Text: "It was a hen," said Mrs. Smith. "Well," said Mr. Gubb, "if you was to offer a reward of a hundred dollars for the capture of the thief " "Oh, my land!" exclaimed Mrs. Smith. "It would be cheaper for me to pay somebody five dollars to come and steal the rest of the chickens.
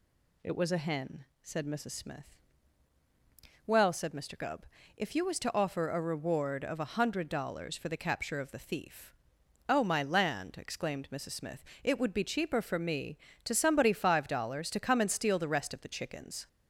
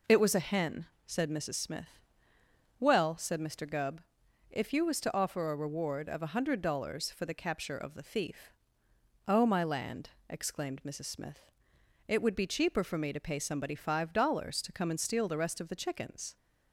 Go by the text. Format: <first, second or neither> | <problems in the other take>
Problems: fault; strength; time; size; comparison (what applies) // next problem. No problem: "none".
second | skips "pay"; at 13.5 s